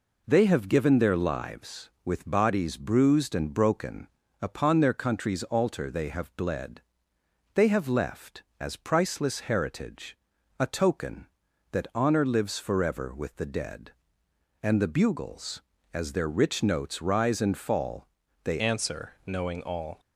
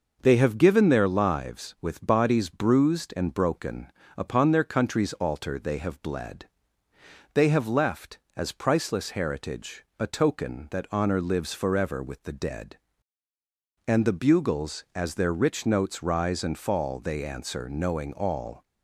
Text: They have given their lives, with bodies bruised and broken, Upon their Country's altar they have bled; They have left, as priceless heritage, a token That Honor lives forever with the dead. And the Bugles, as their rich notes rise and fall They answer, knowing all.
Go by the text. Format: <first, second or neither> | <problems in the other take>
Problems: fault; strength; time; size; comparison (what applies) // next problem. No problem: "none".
second | pauses between "fall" and "They"; at 18.0 s; 0.38 s long // changes voice at "answer"; from 18.5 s on; 1.4 s long